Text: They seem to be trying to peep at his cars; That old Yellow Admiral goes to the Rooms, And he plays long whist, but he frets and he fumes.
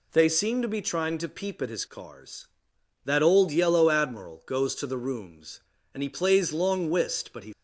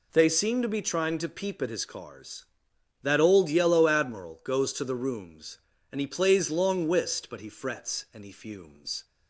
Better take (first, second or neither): second